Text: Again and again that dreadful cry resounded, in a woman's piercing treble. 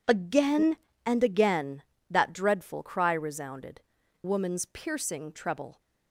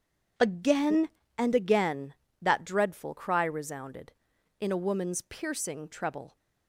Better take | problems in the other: second | skips "in a"; at 4.0 s

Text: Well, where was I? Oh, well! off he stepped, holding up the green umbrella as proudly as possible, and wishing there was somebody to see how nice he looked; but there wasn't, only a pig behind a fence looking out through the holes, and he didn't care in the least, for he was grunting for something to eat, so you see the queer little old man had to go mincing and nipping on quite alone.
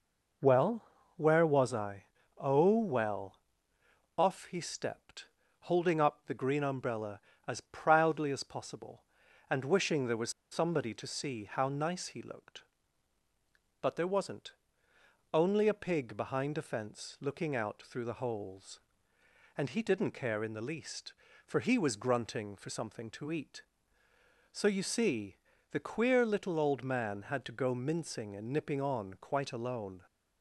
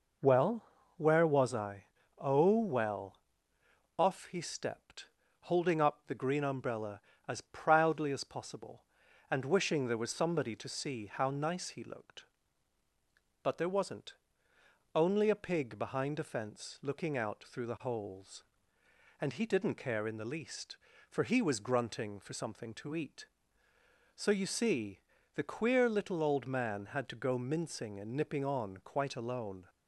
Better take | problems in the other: second | pauses between "was" and "somebody"; slight; at 10.2 s; 0.21 s long // pauses between "see" and "the"; slight; at 25.3 s; 0.34 s long; slight in the second

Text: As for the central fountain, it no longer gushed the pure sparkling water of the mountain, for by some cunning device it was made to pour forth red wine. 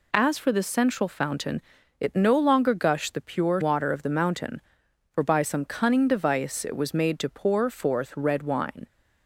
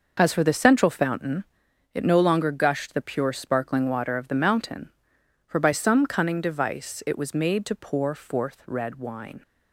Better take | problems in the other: second | skips "sparkling"; at 3.6 s

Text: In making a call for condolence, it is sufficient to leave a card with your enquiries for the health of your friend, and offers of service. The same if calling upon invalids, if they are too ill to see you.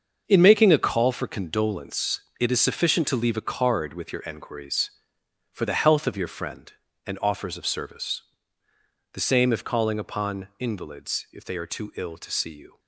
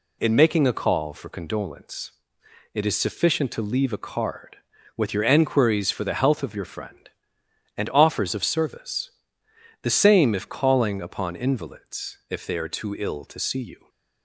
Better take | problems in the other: second | gets quieter; strong; throughout; 10.5 dB

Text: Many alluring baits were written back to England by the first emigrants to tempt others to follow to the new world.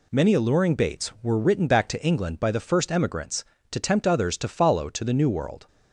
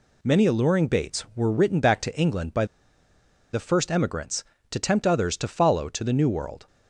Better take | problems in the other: first | pauses between "by" and "the"; noticeable; at 2.6 s; 0.86 s long

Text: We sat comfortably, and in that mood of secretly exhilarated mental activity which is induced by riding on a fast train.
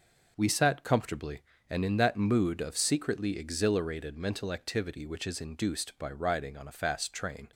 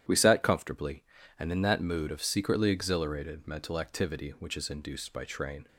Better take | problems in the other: first | starts louder than the rest; strong; until 1.4 s; 11 dB // skips "riding on a fast"; at 5.2 s

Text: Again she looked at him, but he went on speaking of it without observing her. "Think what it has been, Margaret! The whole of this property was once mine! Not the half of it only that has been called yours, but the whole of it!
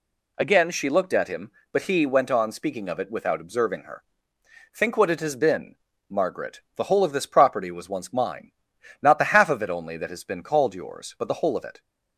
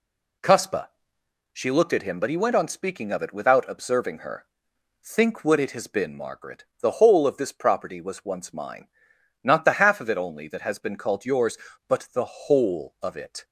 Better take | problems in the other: first | says "Cuspa" for "Again"; at 0.4 s

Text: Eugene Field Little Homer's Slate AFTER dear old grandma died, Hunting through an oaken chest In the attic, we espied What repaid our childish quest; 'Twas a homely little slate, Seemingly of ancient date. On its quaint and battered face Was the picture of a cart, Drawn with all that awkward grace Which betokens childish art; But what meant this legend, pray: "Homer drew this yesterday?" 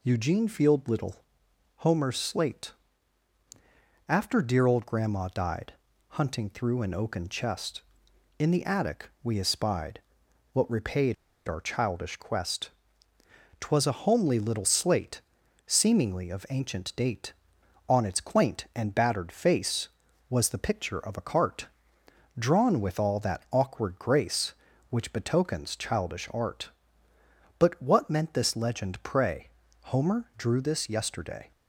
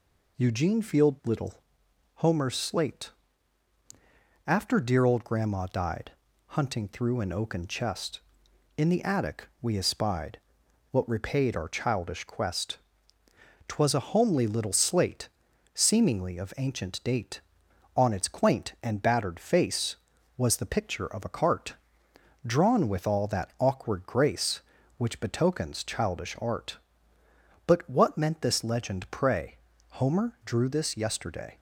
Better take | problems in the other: second | pauses between "Little" and "Homer's"; noticeable; at 1.1 s; 0.60 s long; noticeable in the second // pauses between "Slate" and "AFTER"; strong; at 2.7 s; 1.3 s long; strong in the second // pauses between "espied" and "What"; noticeable; at 10.0 s; 0.52 s long; noticeable in the second // pauses between "repaid" and "our"; slight; at 11.1 s; 0.32 s long

